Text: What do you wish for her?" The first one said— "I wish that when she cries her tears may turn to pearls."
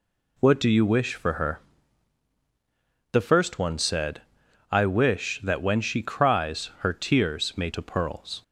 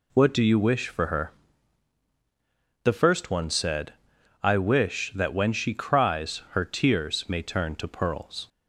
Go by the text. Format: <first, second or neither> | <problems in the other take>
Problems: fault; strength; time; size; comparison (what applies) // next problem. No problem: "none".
second | skips "turn"; at 7.7 s